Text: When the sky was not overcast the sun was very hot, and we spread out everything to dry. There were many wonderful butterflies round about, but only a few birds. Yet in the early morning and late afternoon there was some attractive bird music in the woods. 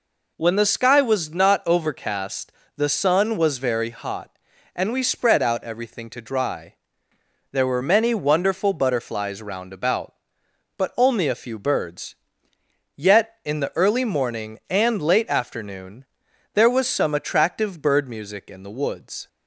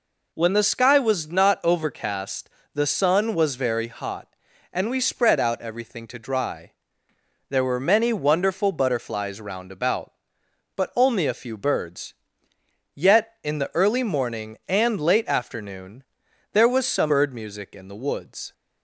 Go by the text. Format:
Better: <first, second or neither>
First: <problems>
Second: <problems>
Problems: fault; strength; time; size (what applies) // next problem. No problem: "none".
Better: first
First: pauses between "overcast" and "the"; slight; at 2.5 s; 0.24 s long // pauses between "afternoon" and "there"; noticeable; at 16.0 s; 0.48 s long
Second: pauses between "overcast" and "the"; slight; at 2.4 s; 0.24 s long // pauses between "afternoon" and "there"; noticeable; at 16.0 s; 0.48 s long // skips "attractive"; at 17.0 s